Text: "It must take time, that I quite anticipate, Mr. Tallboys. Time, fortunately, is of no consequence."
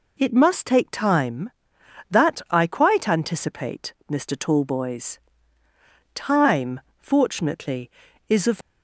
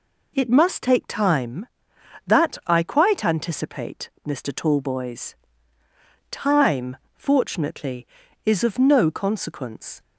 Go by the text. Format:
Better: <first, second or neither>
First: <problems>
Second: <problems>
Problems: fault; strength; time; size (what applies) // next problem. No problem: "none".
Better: second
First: stops before "no consequence"; at 8.6 s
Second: none